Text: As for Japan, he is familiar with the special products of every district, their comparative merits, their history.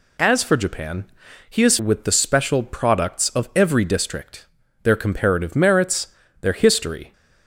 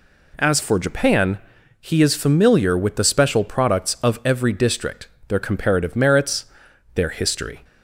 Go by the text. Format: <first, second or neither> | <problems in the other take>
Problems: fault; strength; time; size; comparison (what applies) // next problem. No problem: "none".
second | skips "familiar"; at 1.7 s